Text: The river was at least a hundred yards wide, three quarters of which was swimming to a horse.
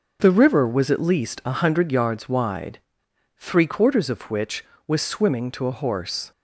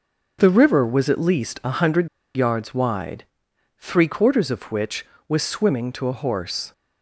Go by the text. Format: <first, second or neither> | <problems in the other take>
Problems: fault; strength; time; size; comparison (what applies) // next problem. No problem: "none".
first | starts louder than the rest; until 1.4 s; 6.5 dB; also in the first // pauses between "hundred" and "yards"; slight; at 2.0 s; 0.27 s long